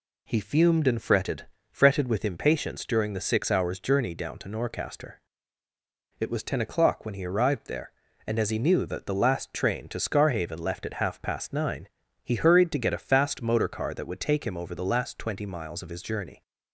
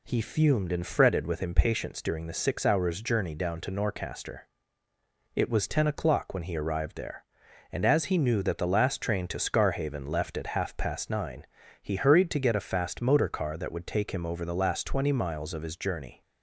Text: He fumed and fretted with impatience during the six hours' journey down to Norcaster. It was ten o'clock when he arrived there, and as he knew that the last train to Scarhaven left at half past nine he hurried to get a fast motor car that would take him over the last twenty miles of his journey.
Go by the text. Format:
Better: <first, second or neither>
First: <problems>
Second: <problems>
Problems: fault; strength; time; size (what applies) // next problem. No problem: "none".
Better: second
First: says "fretted" twice; at 1.6 s // pauses between "nine" and "he"; slight; at 11.8 s; 0.36 s long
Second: pauses between "nine" and "he"; slight; at 11.4 s; 0.36 s long